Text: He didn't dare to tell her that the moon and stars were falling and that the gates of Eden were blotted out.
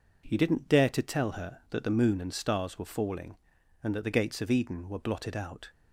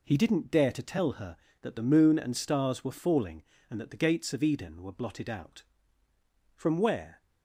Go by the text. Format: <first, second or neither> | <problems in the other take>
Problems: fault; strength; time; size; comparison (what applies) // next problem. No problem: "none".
first | goes on to say "From where"; noticeable; from 6.5 s on; 0.66 s long